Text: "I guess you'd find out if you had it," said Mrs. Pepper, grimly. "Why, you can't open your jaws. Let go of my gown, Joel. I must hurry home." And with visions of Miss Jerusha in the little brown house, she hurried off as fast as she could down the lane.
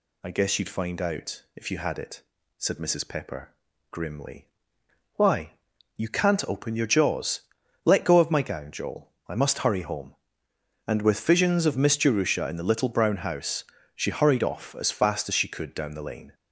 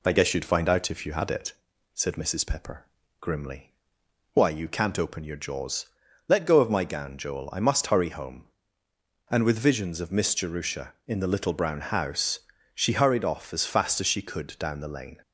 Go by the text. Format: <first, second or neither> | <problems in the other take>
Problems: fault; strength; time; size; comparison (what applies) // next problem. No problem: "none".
neither | none